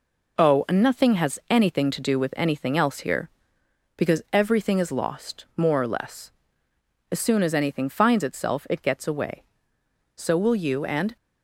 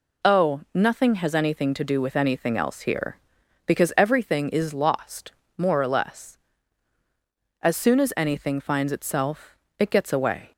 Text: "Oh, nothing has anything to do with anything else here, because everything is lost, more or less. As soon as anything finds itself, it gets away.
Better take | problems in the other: second | goes on to say "So will you and"; noticeable; from 10.1 s on; 1.0 s long

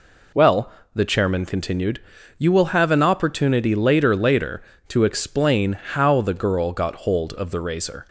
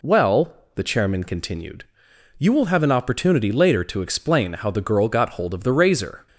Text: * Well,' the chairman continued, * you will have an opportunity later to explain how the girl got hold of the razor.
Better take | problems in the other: second | says "later" twice; at 4.1 s

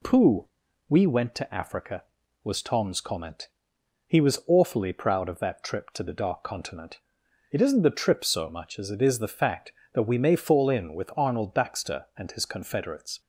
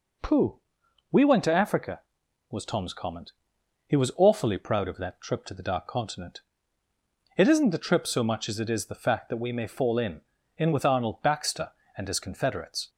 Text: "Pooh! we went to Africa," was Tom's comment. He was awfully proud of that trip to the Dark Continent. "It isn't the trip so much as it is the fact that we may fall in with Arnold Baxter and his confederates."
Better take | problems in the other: first | says "in" twice; at 10.5 s

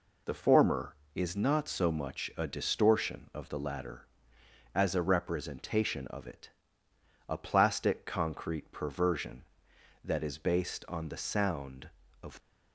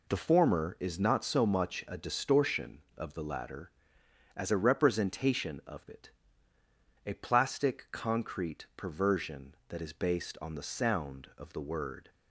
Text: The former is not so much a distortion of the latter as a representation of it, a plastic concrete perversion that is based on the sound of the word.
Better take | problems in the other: second | stops before "the word"; at 12.3 s

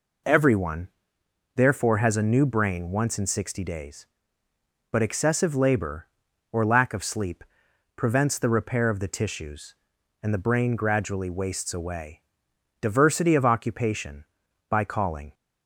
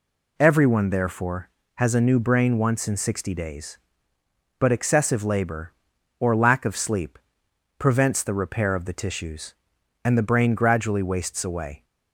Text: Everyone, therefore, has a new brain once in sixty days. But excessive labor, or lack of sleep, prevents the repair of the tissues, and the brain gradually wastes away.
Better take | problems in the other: second | goes on to say "Diversity of occupation by calling"; strong; from 12.7 s on; 2.5 s long

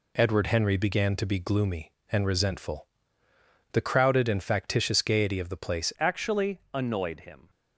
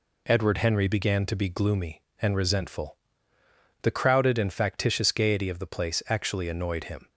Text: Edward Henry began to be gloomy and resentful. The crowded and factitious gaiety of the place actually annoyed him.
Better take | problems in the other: second | changes voice at "actually"; from 5.9 s on; 1.5 s long

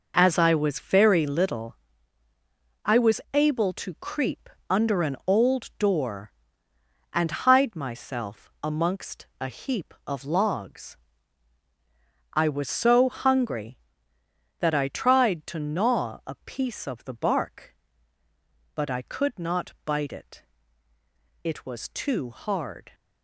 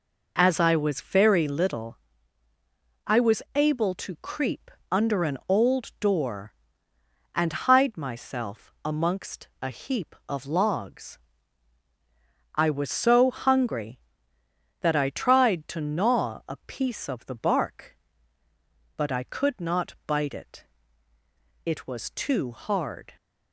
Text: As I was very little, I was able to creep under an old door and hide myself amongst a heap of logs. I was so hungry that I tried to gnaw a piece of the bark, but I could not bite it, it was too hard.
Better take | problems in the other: second | gets quieter; strong; throughout; 10 dB // pauses between "creep" and "under"; slight; at 4.4 s; 0.22 s long; slight in the second // pauses between "amongst" and "a"; slight; at 9.2 s; 0.16 s long; slight in the second

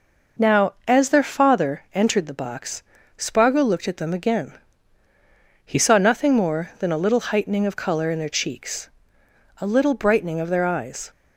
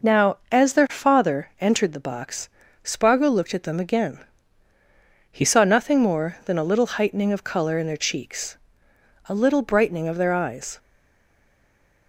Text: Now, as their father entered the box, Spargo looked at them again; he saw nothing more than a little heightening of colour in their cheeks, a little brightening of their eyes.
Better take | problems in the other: first | stays silent after the last word; noticeable; from 10.7 s on; 1.3 s long

